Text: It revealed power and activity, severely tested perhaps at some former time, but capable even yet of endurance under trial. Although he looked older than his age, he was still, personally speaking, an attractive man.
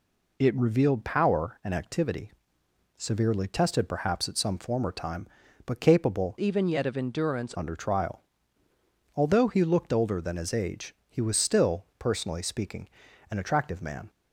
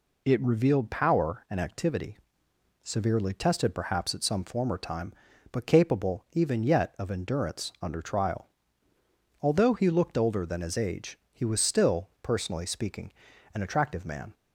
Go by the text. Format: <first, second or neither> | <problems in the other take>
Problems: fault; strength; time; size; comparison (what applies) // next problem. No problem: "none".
second | changes voice from "even" to "endurance"; from 6.3 to 7.5 s; 1.2 s long